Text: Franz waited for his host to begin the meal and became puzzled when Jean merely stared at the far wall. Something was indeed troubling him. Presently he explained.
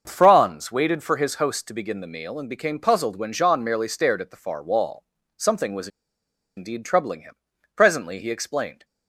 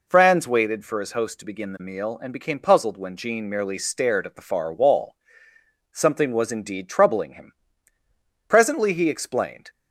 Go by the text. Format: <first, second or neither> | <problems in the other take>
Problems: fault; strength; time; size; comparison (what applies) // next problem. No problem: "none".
second | starts louder than the rest; until 1.0 s; 6.5 dB // pauses between "was" and "indeed"; noticeable; at 5.8 s; 0.68 s long